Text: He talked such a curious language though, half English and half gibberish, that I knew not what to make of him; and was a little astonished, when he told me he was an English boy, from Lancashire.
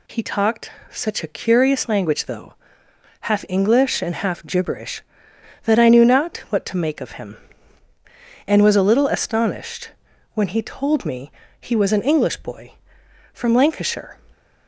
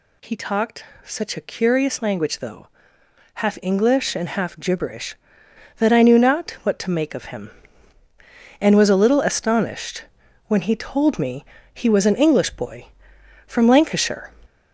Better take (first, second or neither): first